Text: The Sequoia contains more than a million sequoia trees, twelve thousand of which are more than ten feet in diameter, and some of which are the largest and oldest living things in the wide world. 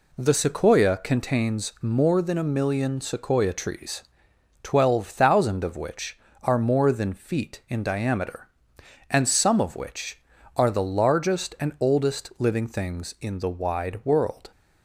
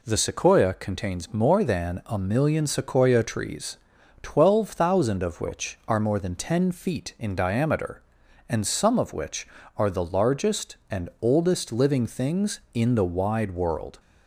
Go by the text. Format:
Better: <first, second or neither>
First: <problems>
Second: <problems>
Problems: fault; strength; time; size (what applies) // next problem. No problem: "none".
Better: second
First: skips "ten"; at 7.1 s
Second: none